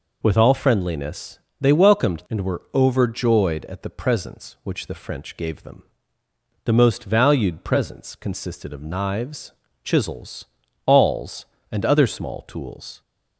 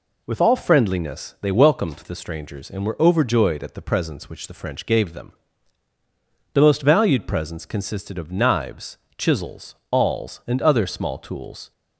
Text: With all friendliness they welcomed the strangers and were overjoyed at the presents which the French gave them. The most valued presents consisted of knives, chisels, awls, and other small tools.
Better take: second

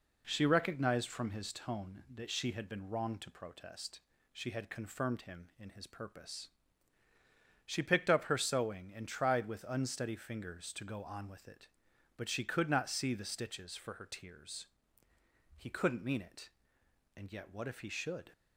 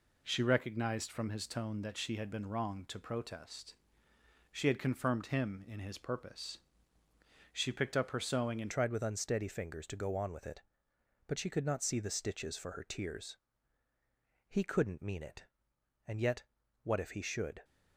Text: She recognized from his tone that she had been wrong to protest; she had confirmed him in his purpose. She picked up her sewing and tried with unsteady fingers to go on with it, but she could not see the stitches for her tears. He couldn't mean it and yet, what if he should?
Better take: first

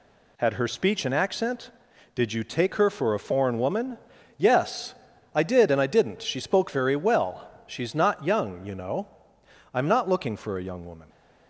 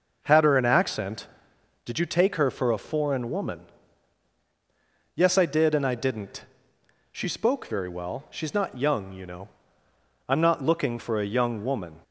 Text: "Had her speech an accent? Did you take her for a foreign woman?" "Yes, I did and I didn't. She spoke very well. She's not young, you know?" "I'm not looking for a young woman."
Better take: first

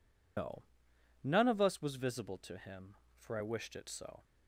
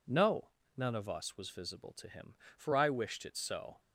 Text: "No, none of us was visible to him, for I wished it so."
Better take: second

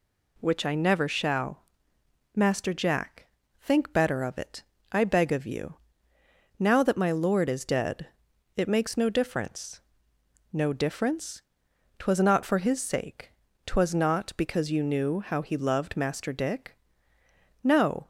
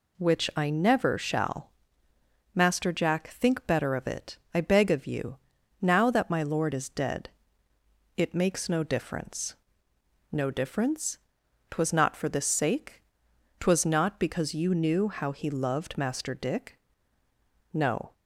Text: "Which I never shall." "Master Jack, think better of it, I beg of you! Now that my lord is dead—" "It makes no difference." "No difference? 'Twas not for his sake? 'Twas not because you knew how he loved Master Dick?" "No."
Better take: first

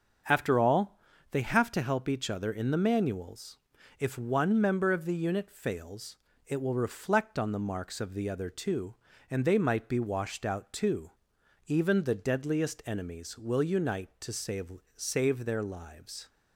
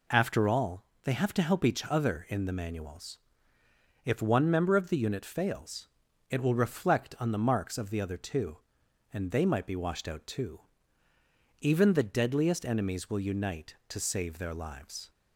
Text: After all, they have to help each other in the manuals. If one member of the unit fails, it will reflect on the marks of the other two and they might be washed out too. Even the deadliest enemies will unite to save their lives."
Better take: second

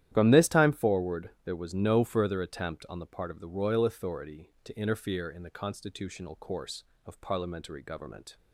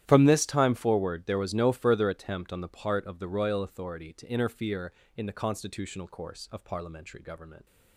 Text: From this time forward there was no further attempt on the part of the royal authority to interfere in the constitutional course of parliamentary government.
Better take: neither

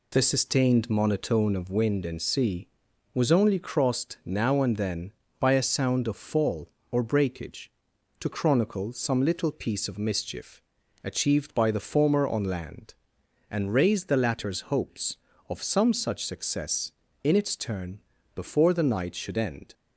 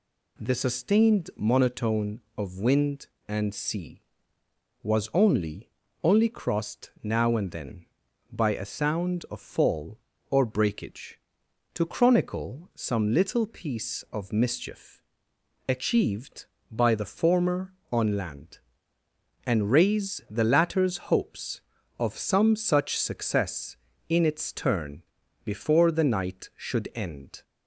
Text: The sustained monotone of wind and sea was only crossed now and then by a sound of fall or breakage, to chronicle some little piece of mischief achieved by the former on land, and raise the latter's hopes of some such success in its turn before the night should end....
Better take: first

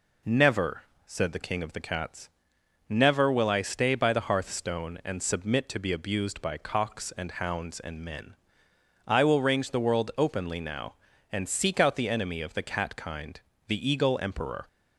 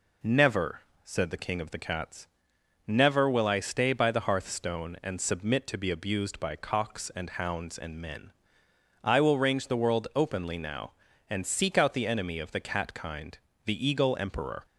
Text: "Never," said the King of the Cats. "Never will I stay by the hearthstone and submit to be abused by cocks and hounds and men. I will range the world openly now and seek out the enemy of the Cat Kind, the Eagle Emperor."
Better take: neither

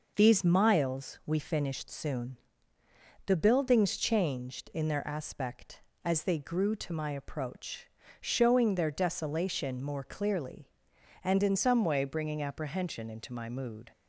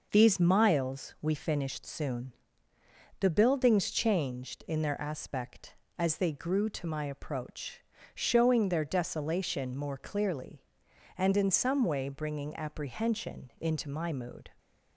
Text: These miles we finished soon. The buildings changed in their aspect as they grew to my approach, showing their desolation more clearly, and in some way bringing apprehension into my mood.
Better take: second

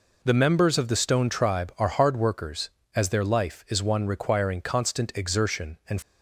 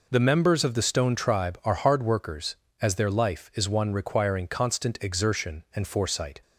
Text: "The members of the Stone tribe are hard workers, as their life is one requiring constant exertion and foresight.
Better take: second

